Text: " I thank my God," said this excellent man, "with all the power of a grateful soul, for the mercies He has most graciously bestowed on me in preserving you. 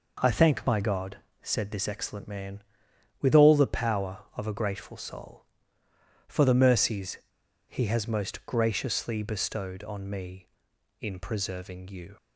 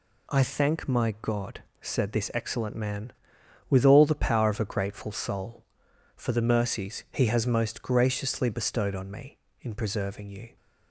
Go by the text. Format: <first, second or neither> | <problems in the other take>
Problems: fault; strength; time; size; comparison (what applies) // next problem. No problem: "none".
second | pauses between "mercies" and "He"; noticeable; at 7.1 s; 0.49 s long